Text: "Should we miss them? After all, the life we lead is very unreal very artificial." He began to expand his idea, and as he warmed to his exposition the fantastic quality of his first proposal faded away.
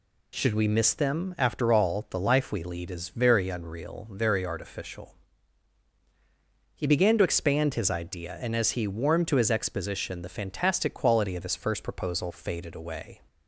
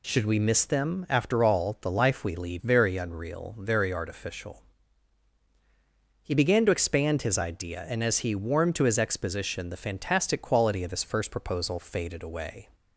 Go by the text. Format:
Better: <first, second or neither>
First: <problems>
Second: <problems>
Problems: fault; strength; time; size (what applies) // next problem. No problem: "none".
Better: first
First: none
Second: skips "is"; at 2.5 s